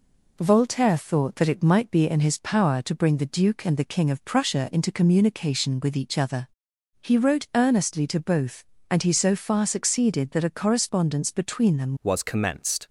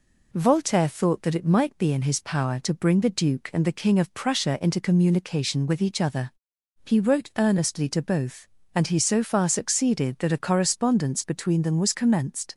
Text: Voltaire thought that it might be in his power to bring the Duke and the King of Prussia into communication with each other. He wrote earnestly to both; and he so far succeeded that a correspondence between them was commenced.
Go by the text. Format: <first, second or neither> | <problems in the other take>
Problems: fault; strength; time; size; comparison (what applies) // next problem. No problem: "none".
second | changes voice at "was"; from 12.0 s on; 0.8 s long